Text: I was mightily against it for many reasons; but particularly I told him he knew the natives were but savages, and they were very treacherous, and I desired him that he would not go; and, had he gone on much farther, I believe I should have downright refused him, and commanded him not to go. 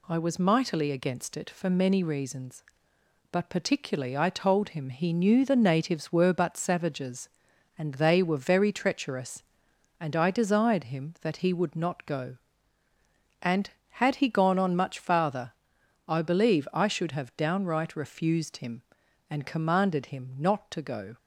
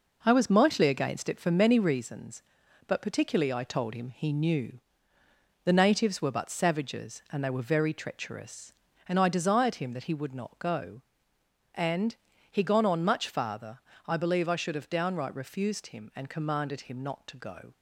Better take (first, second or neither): first